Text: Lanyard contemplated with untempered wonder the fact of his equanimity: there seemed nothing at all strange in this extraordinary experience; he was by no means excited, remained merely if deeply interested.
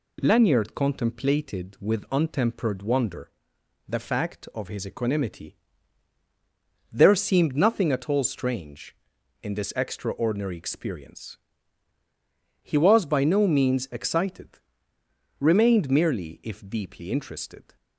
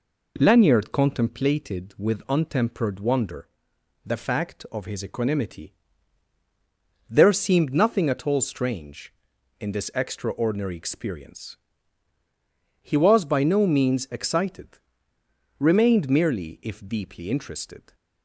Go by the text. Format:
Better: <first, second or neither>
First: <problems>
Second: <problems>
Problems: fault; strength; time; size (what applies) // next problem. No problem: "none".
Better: first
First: pauses between "wonder" and "the"; noticeable; at 3.3 s; 0.56 s long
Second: starts louder than the rest; until 1.3 s; 4 dB // pauses between "wonder" and "the"; noticeable; at 3.4 s; 0.56 s long